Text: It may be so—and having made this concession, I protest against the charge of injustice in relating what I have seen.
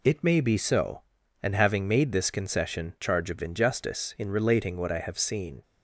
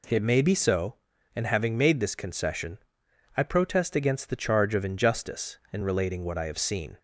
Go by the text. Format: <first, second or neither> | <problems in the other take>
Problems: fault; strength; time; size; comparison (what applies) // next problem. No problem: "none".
second | skips "I protest against the"; at 2.9 s